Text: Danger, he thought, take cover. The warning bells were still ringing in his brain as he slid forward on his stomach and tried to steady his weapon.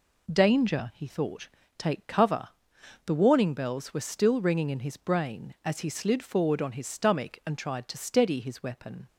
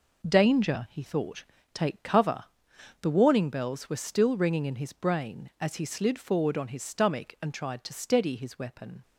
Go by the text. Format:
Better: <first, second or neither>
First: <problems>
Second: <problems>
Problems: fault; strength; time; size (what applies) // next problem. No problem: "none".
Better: first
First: none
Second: gets quieter; strong; throughout; 9 dB